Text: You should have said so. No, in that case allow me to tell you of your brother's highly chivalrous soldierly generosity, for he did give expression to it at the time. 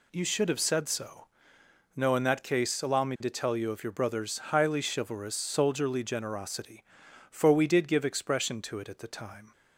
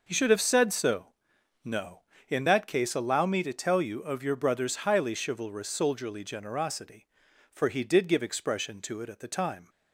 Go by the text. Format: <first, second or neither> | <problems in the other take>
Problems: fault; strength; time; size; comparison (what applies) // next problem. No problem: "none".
second | says "we" for "he"; at 7.5 s